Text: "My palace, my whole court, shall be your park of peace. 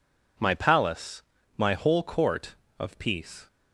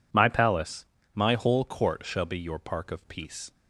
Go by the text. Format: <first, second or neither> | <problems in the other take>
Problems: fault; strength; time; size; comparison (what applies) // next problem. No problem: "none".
second | skips "shall be your park"; at 2.6 s